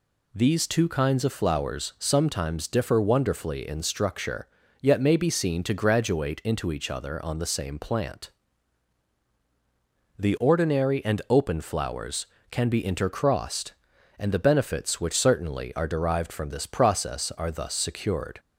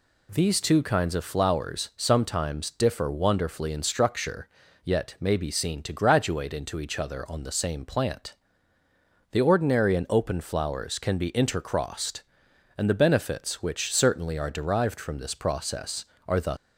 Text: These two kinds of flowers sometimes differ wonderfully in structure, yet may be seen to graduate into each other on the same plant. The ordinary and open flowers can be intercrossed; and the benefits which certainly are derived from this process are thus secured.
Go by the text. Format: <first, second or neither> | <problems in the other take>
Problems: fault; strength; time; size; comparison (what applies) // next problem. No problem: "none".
first | stops before "secured"; at 16.5 s